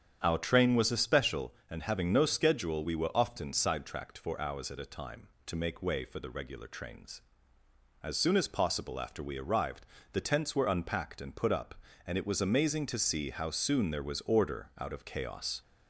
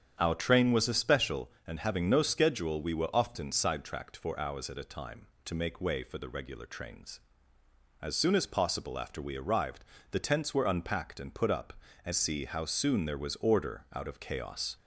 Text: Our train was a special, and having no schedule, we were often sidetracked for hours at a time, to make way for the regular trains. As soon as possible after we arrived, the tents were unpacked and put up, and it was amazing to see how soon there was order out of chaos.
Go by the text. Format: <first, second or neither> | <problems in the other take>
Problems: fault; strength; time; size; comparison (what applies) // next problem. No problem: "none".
first | starts louder than the rest; strong; until 1.2 s; 8.5 dB; strong in the first // skips "it was amazing to"; at 12.1 s